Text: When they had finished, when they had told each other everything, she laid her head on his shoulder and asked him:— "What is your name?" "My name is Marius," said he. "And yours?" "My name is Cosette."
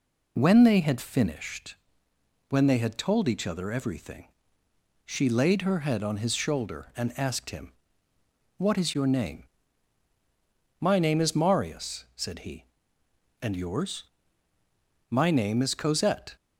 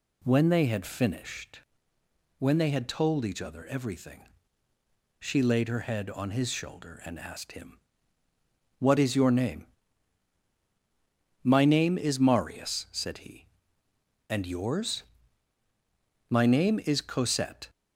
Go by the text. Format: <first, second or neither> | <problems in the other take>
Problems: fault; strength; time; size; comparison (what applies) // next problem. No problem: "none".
neither | none